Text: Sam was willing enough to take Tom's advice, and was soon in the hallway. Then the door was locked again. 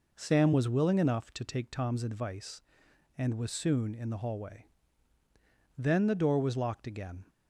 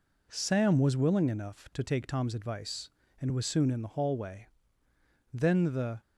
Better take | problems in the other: first | stops before "door was locked again"; at 6.0 s

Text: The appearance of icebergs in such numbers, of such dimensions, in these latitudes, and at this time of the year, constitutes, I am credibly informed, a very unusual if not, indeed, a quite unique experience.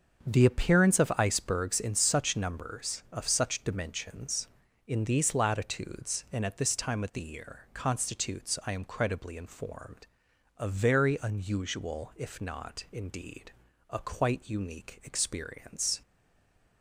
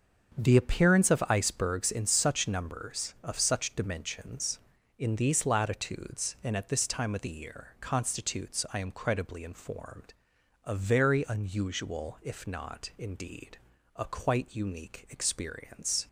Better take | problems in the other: second | starts louder than the rest; until 1.3 s; 7 dB; also in the second // stays silent after the last word; slight; from 16.0 s on; 0.8 s long

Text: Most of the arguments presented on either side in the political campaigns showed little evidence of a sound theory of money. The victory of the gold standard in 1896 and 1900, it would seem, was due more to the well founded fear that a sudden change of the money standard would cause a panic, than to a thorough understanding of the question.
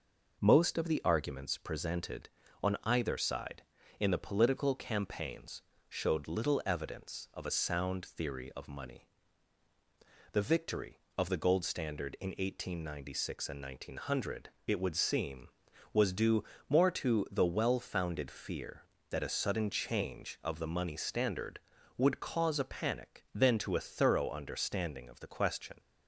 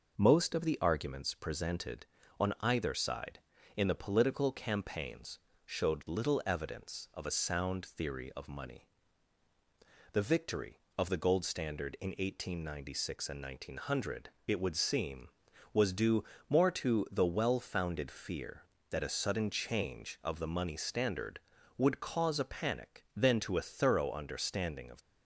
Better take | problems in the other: first | pauses between "campaigns" and "showed"; slight; at 5.3 s; 0.26 s long; slight in the first // pauses between "due" and "more"; slight; at 16.2 s; 0.24 s long; slight in the first // stops before "the question"; at 25.0 s

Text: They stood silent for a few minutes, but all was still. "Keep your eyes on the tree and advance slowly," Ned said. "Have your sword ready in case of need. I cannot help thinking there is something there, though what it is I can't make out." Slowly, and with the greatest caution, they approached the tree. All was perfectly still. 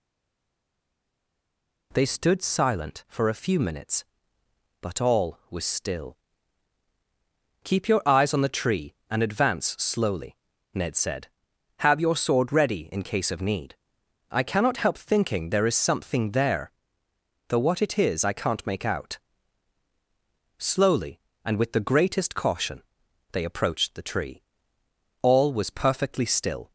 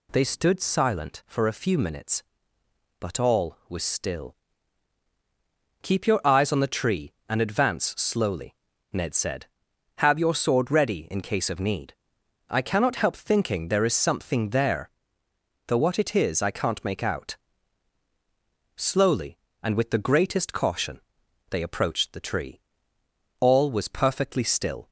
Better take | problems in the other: second | stays silent before the first word; noticeable; until 1.9 s; 1.9 s long

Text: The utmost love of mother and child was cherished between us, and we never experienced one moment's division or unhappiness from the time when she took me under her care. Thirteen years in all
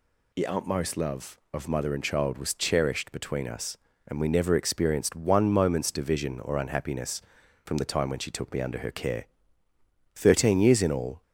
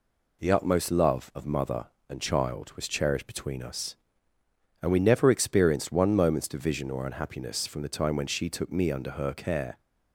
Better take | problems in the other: first | stops before "Thirteen years in all"; at 9.7 s

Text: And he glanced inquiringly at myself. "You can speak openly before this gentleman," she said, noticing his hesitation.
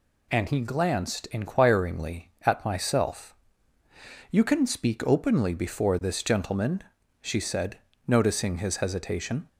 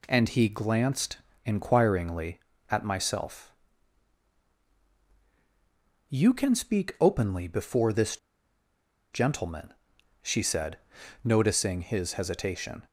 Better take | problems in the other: first | pauses between "glanced" and "inquiringly"; slight; at 1.1 s; 0.26 s long // pauses between "this" and "gentleman"; noticeable; at 8.1 s; 0.96 s long

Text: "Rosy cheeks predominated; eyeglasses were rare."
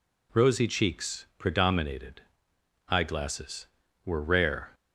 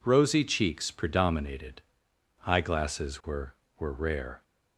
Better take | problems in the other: first | says "were" twice; at 3.7 s

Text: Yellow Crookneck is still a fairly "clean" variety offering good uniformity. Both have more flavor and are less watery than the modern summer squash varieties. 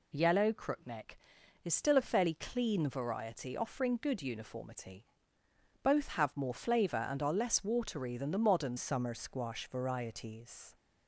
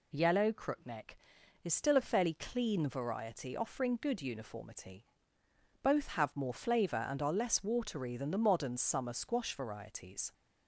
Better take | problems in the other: second | changes voice at "summer"; from 8.7 s on; 2.0 s long

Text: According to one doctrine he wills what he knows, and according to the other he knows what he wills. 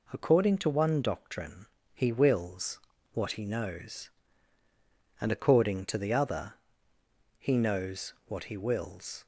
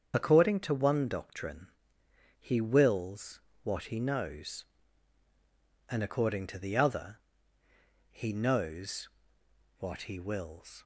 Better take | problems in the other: first | loses the start of "According"; at 0.1 s; 40 ms // starts louder than the rest; strong; until 1.1 s; 7 dB // pauses between "doctrine" and "he"; noticeable; at 1.6 s; 0.68 s long; slight in the first // pauses between "wills" and "what"; slight; at 3.3 s; 0.24 s long; slight in the first // pauses between "other" and "he"; noticeable; at 7.1 s; 0.90 s long; noticeable in the first // pauses between "knows" and "what"; noticeable; at 9.0 s; 0.72 s long

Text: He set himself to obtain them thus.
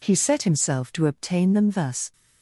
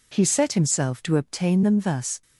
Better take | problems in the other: neither | none

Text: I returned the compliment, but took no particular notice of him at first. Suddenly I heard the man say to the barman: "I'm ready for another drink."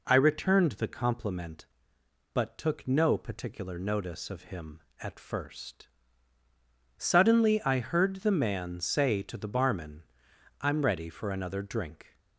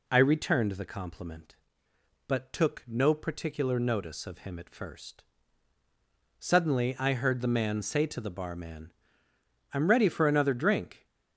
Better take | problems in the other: neither | none

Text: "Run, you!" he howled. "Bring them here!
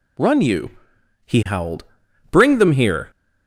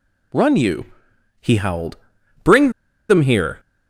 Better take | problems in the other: first | pauses between "Bring" and "them"; at 2.6 s; 0.39 s long

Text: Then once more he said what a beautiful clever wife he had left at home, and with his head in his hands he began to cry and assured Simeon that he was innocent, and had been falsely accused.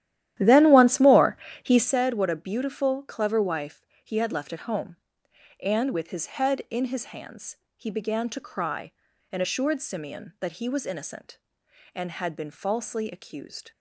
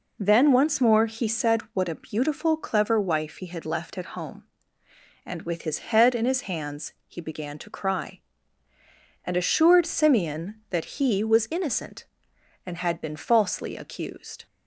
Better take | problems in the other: second | starts louder than the rest; strong; until 1.9 s; 12.5 dB // pauses between "more" and "he"; slight; at 1.3 s; 0.28 s long // pauses between "wife" and "he"; slight; at 3.8 s; 0.22 s long // pauses between "hands" and "he"; slight; at 7.5 s; 0.20 s long

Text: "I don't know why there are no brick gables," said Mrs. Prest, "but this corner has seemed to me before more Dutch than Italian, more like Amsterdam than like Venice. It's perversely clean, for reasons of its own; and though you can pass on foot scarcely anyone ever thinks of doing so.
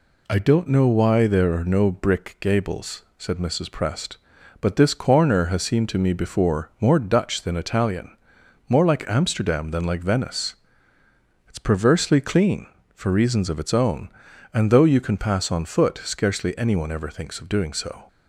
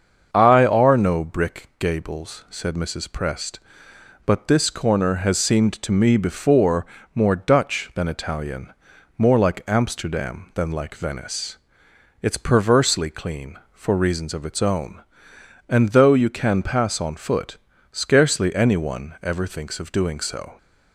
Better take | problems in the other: first | starts louder than the rest; until 1.3 s; 7 dB // skips "don't know why there"; at 0.6 s // pauses between "before" and "more"; slight; at 6.8 s; 0.30 s long // pauses between "foot" and "scarcely"; at 17.5 s; 0.38 s long

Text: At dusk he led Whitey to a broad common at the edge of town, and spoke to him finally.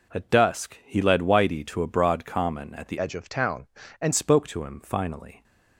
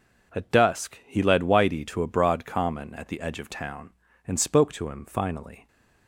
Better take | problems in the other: second | changes voice from "edge" to "and"; from 2.9 to 4.1 s; 1.2 s long

